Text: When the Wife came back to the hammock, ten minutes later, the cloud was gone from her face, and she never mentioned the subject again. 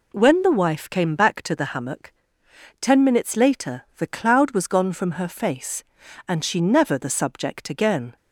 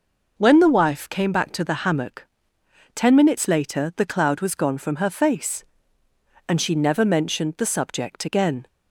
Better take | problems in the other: second | skips "mentioned"; at 6.9 s

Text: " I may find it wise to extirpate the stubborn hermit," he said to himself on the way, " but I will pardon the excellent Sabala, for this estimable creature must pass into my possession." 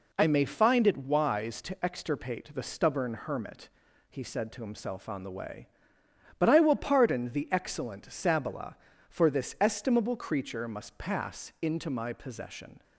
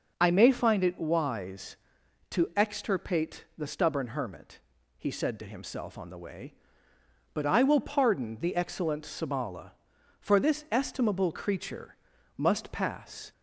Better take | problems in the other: first | starts louder than the rest; until 1.1 s; 6.5 dB // pauses between "creature" and "must"; at 11.9 s; 0.42 s long // stops before "into my possession"; at 13.3 s

